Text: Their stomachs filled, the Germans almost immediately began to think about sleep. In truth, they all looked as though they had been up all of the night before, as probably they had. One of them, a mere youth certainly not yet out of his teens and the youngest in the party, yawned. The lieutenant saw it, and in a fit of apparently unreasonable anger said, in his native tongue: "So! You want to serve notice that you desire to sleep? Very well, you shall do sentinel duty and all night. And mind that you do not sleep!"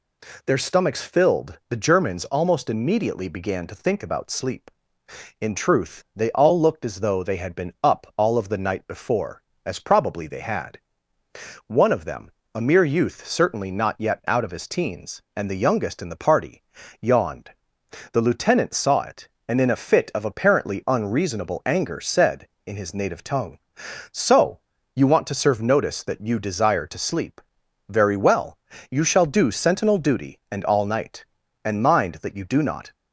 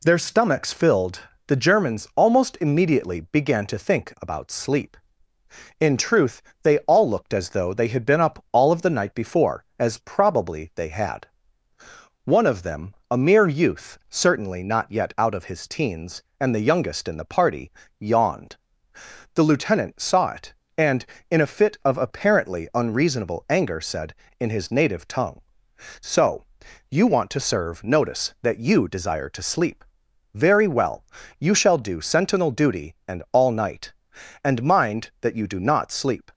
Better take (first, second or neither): second